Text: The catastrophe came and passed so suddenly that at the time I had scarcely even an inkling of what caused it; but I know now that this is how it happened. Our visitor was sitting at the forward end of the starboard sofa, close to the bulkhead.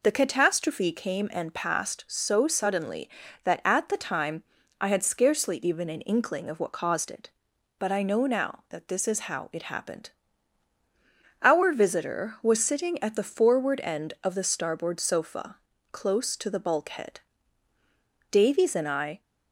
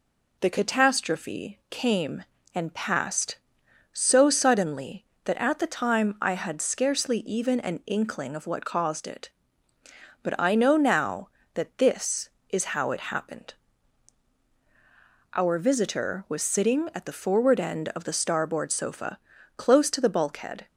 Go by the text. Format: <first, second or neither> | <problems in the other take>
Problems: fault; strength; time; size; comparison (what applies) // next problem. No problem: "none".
second | pauses between "time" and "I"; at 4.4 s; 0.38 s long // goes on to say "Davies and I"; noticeable; from 18.3 s on; 0.90 s long